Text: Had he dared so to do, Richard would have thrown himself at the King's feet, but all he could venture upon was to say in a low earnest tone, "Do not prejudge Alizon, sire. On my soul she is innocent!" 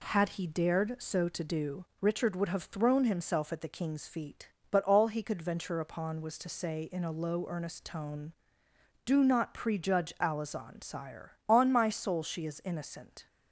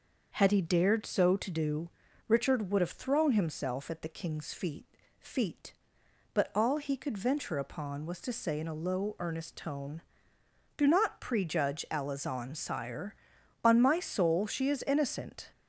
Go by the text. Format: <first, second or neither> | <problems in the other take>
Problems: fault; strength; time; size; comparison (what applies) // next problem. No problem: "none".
first | starts louder than the rest; until 1.3 s; 6 dB // says "feet" twice; at 5.1 s